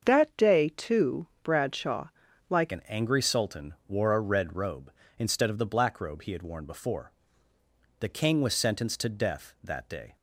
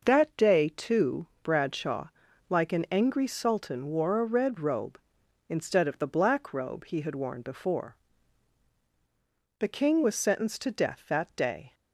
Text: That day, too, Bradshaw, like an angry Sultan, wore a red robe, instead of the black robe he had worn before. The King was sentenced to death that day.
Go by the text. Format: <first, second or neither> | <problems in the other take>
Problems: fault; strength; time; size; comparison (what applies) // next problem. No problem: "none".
second | starts louder than the rest; until 1.1 s; 7 dB // changes voice at "an"; from 2.7 s on; 7.4 s long